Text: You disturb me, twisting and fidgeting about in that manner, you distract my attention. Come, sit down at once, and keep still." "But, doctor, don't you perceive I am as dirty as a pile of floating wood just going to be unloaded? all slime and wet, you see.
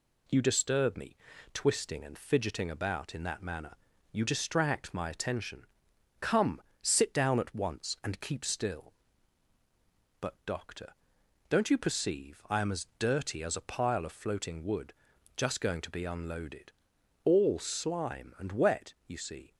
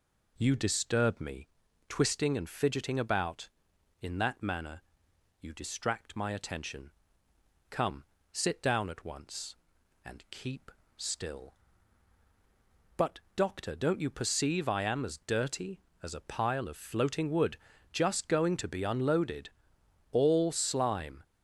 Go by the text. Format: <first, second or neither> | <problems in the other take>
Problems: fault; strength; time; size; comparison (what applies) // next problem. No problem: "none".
first | pauses between "keep" and "still"; slight; at 10.7 s; 0.24 s long // pauses between "wood" and "just"; slight; at 17.5 s; 0.34 s long; also in the first // stops before "and wet you see"; at 21.2 s